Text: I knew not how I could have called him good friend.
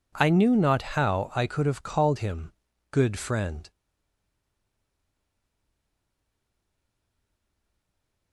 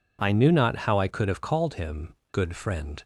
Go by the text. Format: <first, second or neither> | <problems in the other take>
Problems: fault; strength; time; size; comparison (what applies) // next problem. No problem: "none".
second | pauses between "him" and "good"; at 2.5 s; 0.40 s long; slight in the second // stays silent after the last word; strong; from 3.7 s on; 4.6 s long